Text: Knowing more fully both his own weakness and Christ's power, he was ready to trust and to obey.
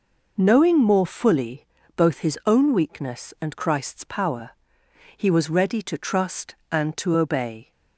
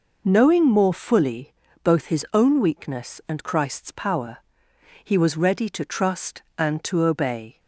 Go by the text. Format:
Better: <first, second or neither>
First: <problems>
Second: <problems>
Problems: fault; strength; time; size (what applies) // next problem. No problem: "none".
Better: neither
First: pauses between "fully" and "both"; slight; at 1.6 s; 0.32 s long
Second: pauses between "fully" and "both"; slight; at 1.5 s; 0.32 s long